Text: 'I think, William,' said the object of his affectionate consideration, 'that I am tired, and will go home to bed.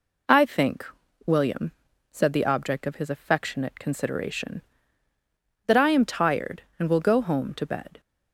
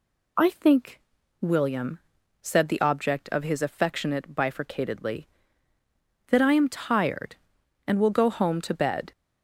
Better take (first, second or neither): first